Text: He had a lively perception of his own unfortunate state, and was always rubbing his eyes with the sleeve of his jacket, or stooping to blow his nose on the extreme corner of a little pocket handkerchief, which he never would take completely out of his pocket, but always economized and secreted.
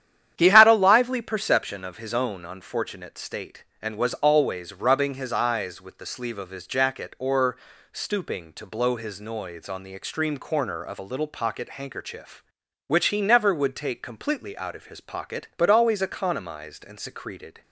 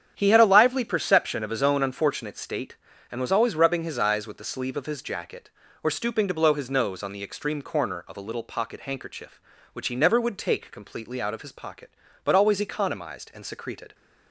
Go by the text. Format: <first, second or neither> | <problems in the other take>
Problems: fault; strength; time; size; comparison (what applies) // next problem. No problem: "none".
second | starts louder than the rest; strong; until 1.3 s; 10 dB; strong in the second // pauses between "or" and "stooping"; slight; at 7.5 s; 0.34 s long // says "noise" for "nose"; at 9.1 s